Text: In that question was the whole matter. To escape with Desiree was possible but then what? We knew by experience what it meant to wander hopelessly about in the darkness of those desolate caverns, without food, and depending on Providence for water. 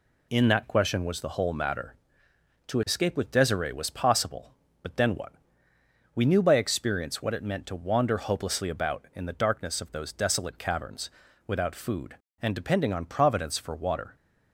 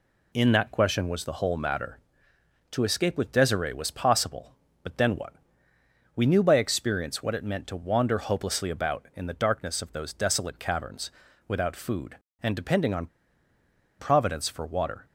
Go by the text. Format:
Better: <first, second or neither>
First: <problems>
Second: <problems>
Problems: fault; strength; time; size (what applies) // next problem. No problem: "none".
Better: first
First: none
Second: pauses between "on" and "Providence"; noticeable; at 13.0 s; 0.92 s long